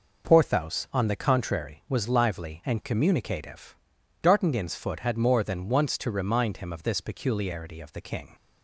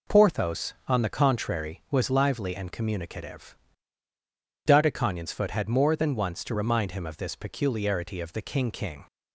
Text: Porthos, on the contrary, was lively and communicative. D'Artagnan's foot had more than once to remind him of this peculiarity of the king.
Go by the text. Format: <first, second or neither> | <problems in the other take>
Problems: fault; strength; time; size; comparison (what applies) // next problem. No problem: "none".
first | says "king" twice; at 8.7 s